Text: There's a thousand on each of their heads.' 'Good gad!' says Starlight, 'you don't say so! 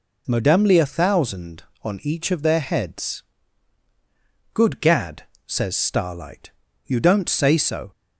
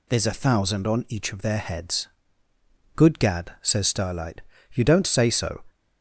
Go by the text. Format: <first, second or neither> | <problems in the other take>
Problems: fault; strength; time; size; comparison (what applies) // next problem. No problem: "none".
second | says "Modemly" for "There's"; at 0.2 s